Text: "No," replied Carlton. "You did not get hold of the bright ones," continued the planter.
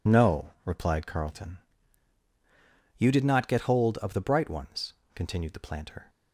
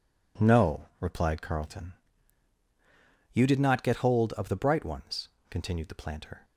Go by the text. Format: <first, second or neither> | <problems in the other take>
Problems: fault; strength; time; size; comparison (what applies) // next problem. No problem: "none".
second | loses the start of "No"; at 0.0 s; 55 ms